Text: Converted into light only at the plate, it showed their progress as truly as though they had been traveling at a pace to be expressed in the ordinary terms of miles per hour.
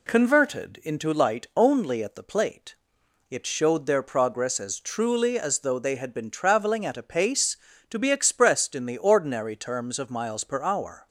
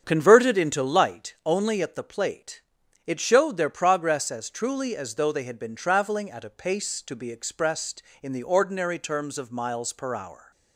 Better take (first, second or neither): first